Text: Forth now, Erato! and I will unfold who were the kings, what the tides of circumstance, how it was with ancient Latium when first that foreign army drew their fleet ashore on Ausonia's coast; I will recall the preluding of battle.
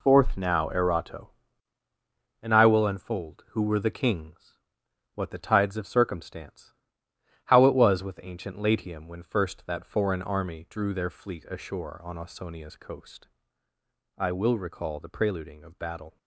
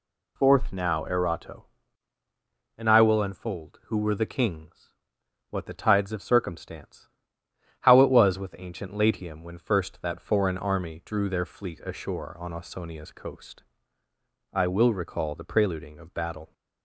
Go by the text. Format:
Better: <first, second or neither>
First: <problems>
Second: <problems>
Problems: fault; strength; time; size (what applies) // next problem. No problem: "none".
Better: second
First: gets quieter; strong; throughout; 8.5 dB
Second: none